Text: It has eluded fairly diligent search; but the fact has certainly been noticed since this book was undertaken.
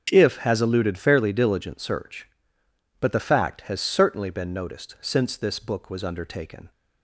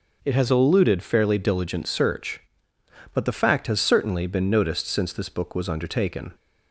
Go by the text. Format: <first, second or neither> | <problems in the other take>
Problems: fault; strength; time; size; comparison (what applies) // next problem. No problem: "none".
second | starts louder than the rest; strong; until 1.1 s; 7.5 dB; noticeable in the second // says "If" for "It"; at 0.1 s